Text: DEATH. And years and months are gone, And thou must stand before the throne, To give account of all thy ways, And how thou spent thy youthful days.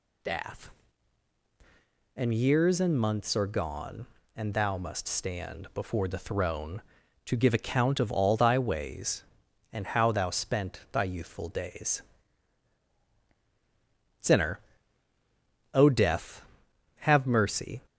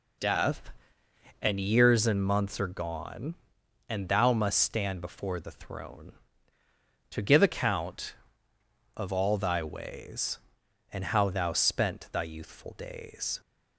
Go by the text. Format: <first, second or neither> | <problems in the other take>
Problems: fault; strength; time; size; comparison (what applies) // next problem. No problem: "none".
second | goes on to say "SINNER O Death have mercy"; strong; from 14.2 s on; 3.6 s long